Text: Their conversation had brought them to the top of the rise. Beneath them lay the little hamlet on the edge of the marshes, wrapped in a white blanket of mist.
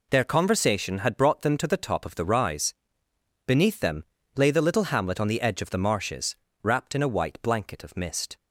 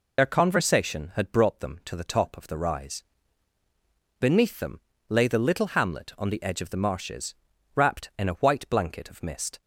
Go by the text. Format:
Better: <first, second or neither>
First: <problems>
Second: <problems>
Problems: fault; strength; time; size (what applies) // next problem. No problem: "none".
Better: first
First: pauses between "them" and "lay"; slight; at 4.0 s; 0.34 s long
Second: loses the start of "Their"; at 0.1 s; 55 ms // pauses between "them" and "lay"; slight; at 4.8 s; 0.28 s long